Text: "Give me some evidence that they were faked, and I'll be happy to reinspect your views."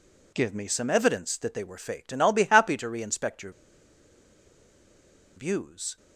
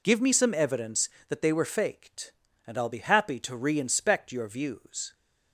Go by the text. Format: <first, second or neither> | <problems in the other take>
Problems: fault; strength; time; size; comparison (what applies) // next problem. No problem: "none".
second | pauses between "your" and "views"; strong; at 3.5 s; 1.8 s long